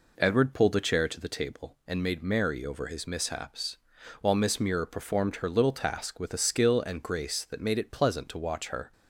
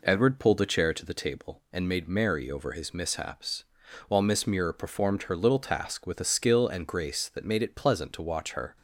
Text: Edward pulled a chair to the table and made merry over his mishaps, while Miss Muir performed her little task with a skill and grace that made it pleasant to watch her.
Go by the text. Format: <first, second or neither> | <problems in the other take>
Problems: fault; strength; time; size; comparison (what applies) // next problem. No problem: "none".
neither | none